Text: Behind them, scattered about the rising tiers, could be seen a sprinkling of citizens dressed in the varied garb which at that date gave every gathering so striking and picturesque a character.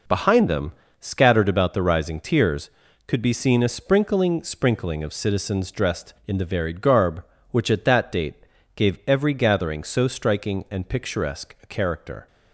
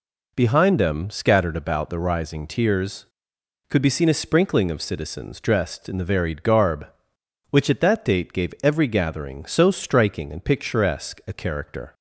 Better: second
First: says "sprinkling" twice; at 4.4 s // pauses between "date" and "gave"; at 8.3 s; 0.40 s long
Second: none

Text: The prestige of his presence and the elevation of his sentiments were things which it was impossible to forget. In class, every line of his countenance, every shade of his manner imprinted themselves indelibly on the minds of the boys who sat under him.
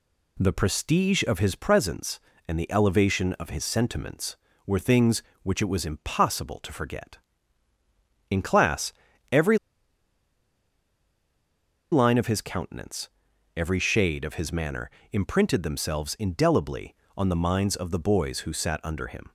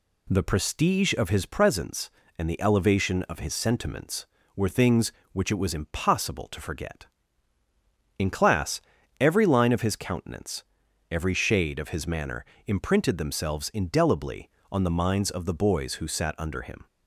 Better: second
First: pauses between "every" and "line"; strong; at 9.5 s; 2.3 s long // pauses between "manner" and "imprinted"; slight; at 14.8 s; 0.22 s long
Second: pauses between "manner" and "imprinted"; slight; at 12.4 s; 0.22 s long

